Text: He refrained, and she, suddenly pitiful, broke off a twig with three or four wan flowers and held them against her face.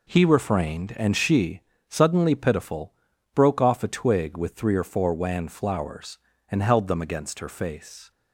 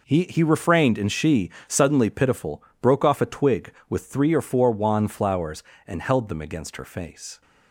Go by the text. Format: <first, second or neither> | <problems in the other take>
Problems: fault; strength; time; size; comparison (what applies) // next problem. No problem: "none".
first | says "He" twice; at 0.2 s